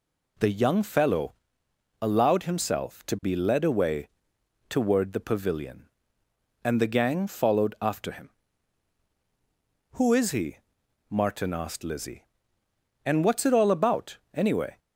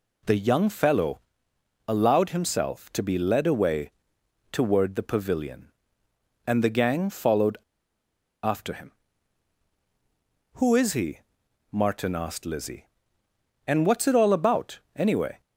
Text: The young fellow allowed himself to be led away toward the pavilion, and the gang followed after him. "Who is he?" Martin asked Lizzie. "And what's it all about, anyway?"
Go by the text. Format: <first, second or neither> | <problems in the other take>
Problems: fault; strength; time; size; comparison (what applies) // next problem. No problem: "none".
first | pauses between "fellow" and "allowed"; noticeable; at 1.1 s; 0.66 s long; noticeable in the first // pauses between "away" and "toward"; noticeable; at 3.9 s; 0.62 s long; noticeable in the first // pauses between "followed" and "after"; noticeable; at 7.5 s; 0.85 s long